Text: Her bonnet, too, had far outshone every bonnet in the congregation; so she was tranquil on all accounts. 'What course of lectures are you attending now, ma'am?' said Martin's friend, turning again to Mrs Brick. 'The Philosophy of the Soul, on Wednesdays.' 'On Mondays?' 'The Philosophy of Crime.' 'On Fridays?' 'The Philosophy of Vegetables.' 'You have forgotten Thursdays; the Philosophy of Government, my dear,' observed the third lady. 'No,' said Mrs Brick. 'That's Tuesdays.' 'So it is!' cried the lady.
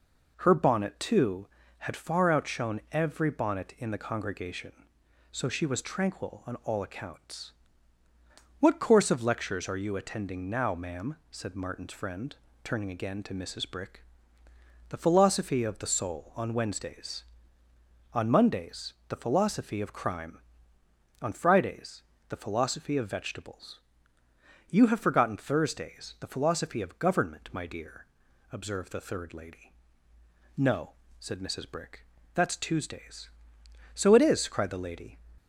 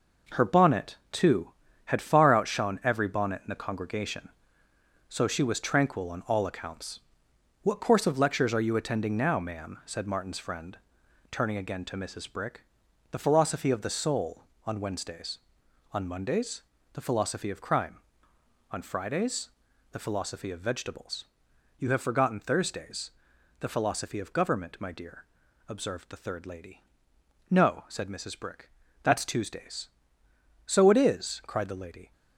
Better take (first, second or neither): first